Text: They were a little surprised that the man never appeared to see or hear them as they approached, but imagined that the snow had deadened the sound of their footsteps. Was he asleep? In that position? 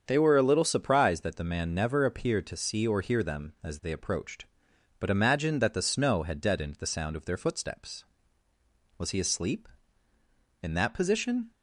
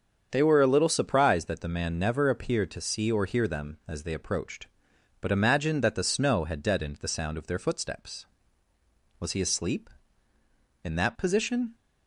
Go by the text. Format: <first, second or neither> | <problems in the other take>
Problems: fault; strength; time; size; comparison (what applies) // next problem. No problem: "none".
neither | starts louder than the rest; strong; the same in both